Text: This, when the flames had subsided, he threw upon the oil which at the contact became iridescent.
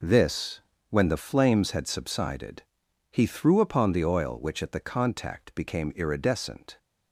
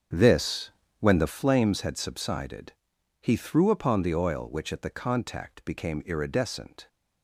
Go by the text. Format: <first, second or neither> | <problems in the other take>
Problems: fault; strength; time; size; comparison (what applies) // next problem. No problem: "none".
first | starts louder than the rest; strong; until 1.5 s; 7.5 dB